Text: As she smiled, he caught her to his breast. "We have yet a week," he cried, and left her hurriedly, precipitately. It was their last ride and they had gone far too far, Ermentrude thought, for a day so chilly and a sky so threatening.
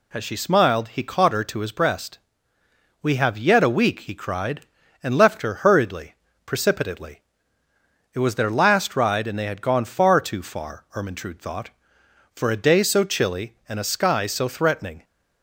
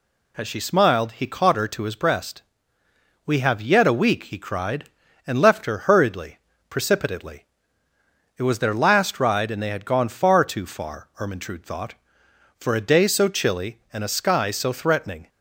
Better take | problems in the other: neither | none

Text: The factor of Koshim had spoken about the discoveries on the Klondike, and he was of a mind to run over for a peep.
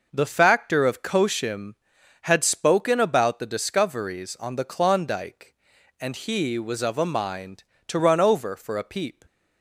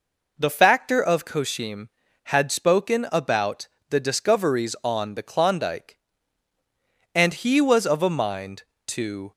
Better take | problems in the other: first | pauses between "about" and "the"; slight; at 3.6 s; 0.22 s long // stops before "run over for a peep"; at 9.3 s

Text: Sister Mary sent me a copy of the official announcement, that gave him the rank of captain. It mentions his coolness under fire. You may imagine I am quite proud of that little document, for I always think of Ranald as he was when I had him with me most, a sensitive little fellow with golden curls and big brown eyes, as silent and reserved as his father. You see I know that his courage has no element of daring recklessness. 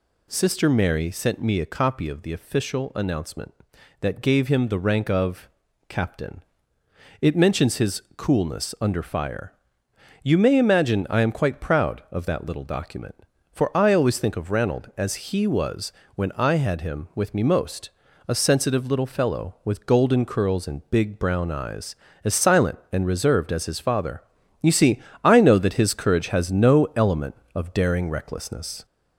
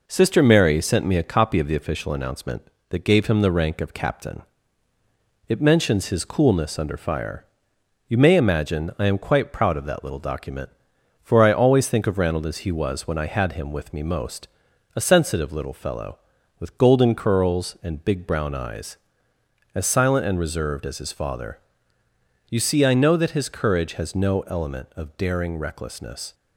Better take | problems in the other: second | gets louder; slight; throughout; 3 dB // pauses between "of" and "captain"; at 5.4 s; 0.40 s long // pauses between "was" and "when"; slight; at 15.9 s; 0.24 s long // pauses between "see" and "I"; slight; at 24.9 s; 0.26 s long

